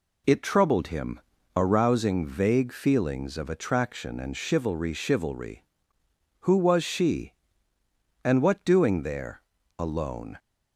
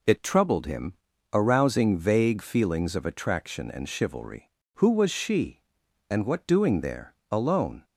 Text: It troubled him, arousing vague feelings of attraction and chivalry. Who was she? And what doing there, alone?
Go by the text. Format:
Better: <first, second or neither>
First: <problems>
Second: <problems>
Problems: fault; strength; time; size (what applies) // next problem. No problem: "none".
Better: second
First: says "chivalry" twice; at 4.9 s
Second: none